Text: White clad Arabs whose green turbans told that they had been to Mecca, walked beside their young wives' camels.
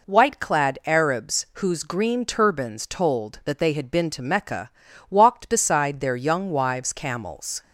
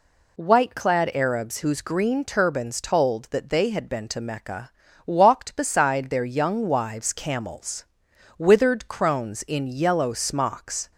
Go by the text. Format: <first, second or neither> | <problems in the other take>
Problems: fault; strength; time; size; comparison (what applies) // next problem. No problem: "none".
first | goes on to say "Withered crones in yellow smocks"; strong; from 8.3 s on; 2.5 s long